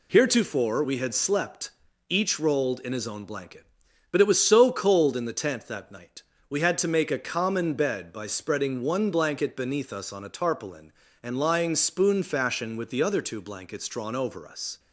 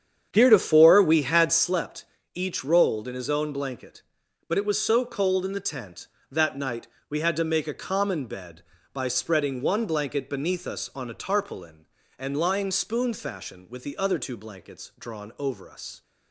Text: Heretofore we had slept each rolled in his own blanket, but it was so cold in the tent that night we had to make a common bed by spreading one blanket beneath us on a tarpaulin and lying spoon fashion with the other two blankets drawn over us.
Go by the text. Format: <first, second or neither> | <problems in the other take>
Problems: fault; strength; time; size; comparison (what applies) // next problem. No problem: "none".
first | starts louder than the rest; strong; until 1.7 s; 8.5 dB // pauses between "slept" and "each"; slight; at 2.0 s; 0.30 s long; also in the first // pauses between "night" and "we"; slight; at 6.8 s; 0.22 s long; slight in the first